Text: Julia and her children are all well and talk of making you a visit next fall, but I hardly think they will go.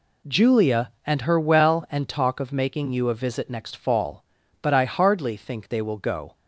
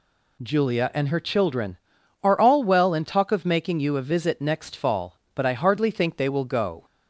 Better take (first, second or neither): second